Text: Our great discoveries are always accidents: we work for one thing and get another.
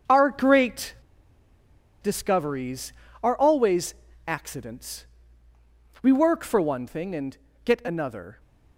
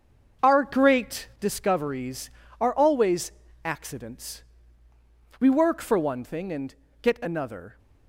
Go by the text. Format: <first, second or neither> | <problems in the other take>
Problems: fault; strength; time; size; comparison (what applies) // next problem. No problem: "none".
second | starts louder than the rest; until 2.1 s; 6.5 dB; also in the second // pauses between "great" and "discoveries"; at 0.9 s; 1.0 s long // pauses between "always" and "accidents"; slight; at 3.9 s; 0.32 s long; slight in the second // pauses between "and" and "get"; slight; at 7.3 s; 0.30 s long; slight in the second